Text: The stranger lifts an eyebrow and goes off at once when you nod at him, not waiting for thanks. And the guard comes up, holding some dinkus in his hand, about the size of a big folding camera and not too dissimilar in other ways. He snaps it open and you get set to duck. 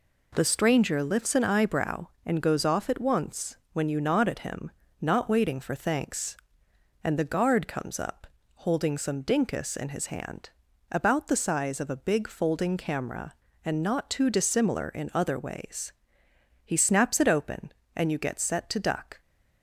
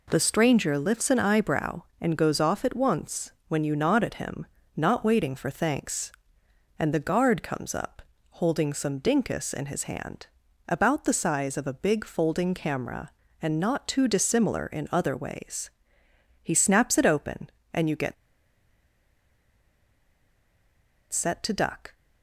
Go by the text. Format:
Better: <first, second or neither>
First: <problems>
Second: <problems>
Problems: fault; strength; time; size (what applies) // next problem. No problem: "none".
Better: first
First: pauses between "once" and "when"; slight; at 3.5 s; 0.18 s long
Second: pauses between "once" and "when"; slight; at 3.3 s; 0.18 s long // pauses between "get" and "set"; strong; at 18.1 s; 2.9 s long